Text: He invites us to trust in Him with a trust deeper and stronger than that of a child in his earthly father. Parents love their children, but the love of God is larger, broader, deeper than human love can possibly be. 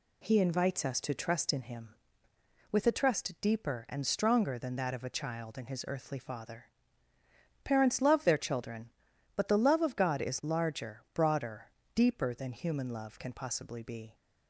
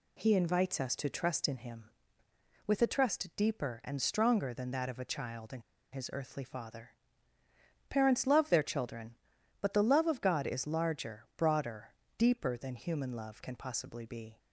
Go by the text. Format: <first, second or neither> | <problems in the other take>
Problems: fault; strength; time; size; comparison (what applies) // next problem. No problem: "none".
first | pauses between "in" and "his"; slight; at 5.6 s; 0.30 s long